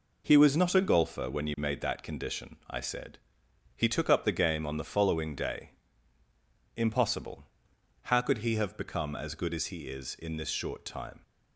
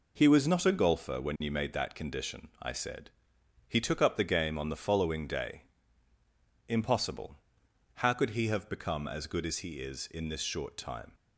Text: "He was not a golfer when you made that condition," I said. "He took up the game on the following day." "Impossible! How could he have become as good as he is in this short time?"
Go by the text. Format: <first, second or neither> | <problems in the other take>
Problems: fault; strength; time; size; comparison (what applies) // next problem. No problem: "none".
neither | none